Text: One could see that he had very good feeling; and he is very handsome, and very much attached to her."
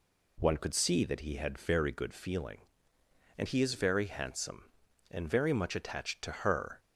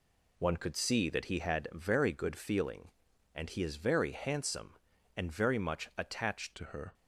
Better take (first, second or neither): first